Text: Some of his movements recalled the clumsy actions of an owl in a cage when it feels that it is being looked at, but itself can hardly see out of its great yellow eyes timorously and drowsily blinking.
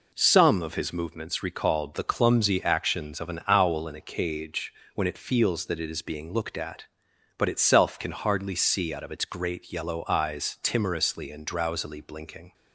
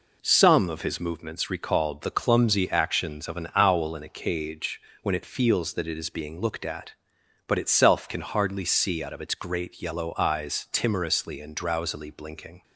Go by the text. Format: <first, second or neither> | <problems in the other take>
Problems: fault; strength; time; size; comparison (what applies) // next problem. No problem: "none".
neither | pauses between "cage" and "when"; slight; the same in both